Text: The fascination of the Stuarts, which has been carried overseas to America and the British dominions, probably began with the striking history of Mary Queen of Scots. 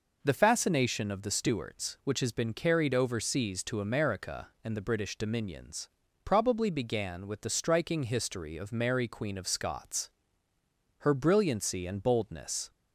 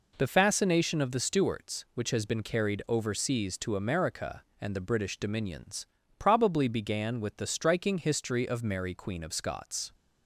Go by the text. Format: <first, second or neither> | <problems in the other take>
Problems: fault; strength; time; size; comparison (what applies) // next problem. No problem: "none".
second | goes on to say "Her brilliancy and boldness"; strong; from 10.9 s on; 1.7 s long